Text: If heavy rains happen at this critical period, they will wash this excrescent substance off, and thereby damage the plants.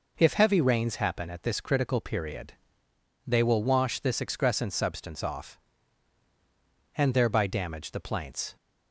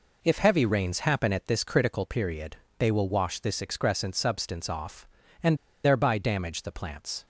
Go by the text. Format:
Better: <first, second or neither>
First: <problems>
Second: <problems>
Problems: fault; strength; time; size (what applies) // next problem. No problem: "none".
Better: first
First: none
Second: pauses between "and" and "thereby"; slight; at 5.5 s; 0.28 s long